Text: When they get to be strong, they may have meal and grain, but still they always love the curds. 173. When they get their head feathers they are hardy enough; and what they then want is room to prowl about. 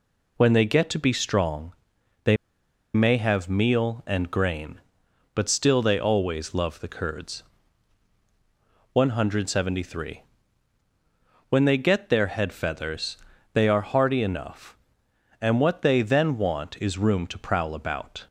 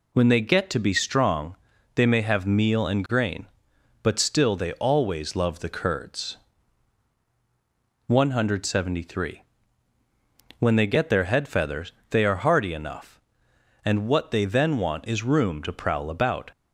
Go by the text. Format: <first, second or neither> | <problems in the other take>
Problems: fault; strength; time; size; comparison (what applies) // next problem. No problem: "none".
second | pauses between "they" and "may"; noticeable; at 2.3 s; 0.58 s long // pauses between "feathers" and "they"; at 13.1 s; 0.38 s long; slight in the second